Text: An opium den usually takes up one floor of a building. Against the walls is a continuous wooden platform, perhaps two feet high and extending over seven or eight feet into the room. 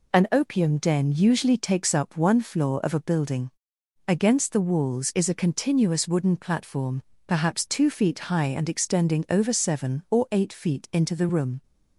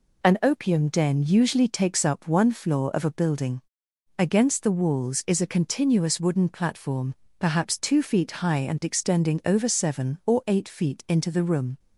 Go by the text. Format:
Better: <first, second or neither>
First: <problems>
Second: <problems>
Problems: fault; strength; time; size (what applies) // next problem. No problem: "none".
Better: neither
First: none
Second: none